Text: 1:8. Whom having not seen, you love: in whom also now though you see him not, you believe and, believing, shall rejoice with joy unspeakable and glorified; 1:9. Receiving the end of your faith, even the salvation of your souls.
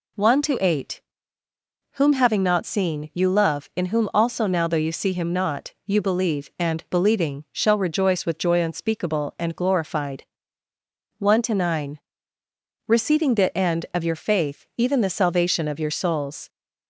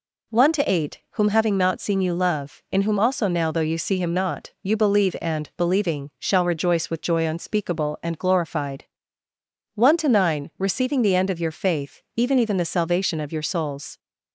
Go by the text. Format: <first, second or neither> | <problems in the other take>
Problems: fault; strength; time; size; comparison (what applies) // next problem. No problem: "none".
first | says "even" twice; at 12.4 s